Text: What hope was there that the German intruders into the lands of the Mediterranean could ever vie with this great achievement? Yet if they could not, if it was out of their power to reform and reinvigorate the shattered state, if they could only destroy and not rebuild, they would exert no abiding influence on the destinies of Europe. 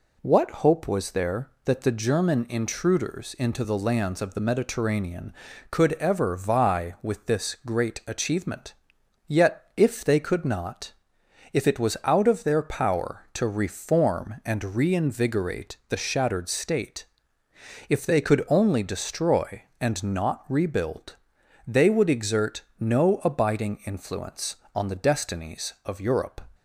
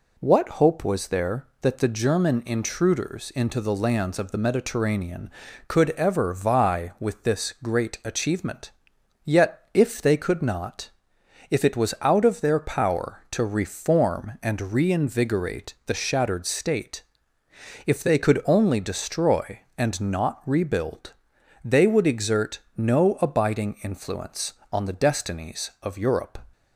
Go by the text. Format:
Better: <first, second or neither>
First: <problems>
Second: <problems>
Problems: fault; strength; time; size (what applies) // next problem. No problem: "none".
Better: neither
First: pauses between "exert" and "no"; slight; at 22.6 s; 0.18 s long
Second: pauses between "exert" and "no"; slight; at 22.5 s; 0.18 s long